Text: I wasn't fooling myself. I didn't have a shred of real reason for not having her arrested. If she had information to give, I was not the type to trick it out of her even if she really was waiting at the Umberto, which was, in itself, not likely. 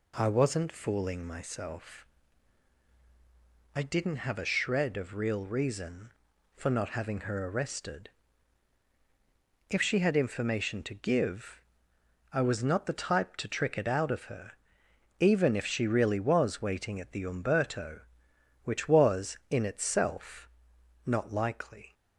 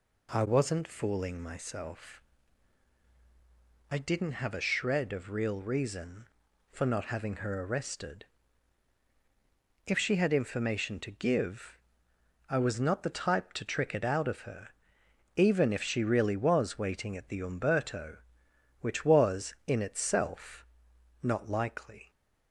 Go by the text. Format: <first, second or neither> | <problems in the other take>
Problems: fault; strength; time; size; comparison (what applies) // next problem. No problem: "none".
neither | pauses between "her" and "even"; noticeable; the same in both